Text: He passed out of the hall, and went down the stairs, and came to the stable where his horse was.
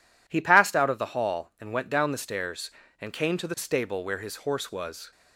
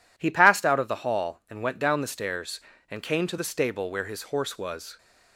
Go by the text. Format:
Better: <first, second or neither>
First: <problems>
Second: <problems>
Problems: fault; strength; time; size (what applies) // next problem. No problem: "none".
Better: neither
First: none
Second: none